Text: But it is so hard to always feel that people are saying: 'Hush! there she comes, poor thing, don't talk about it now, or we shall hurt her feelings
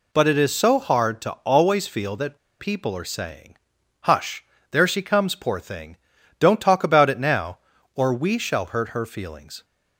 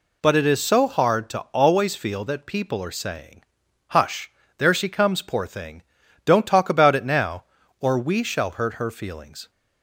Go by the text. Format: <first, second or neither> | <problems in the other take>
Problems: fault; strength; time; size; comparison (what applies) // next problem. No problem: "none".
second | pauses between "that" and "people"; slight; at 2.3 s; 0.22 s long